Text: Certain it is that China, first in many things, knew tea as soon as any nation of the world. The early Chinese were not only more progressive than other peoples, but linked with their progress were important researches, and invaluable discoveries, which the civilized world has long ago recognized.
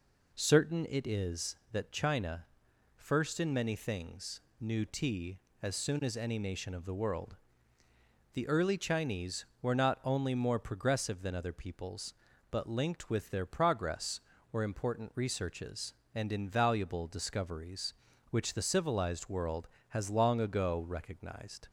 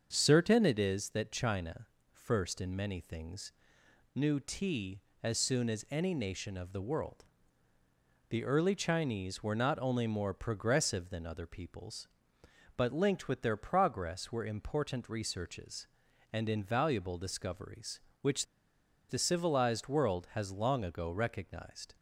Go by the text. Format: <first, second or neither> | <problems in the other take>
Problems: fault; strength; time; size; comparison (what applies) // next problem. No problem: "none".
first | starts louder than the rest; until 1.1 s; 6.5 dB // pauses between "which" and "the"; noticeable; at 18.4 s; 0.65 s long